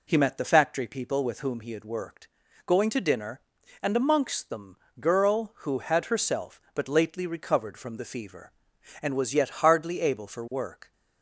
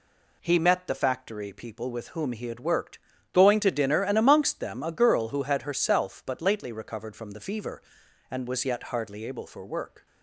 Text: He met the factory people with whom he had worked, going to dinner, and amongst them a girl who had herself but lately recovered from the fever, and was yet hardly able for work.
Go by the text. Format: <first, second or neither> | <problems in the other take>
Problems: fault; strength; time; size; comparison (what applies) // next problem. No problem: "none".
second | skips "a"; at 4.8 s